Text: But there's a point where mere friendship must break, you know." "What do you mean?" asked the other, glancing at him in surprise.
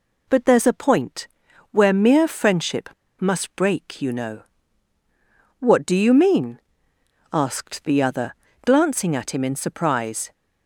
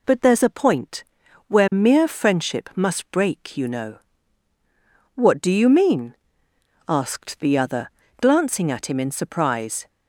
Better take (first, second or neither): second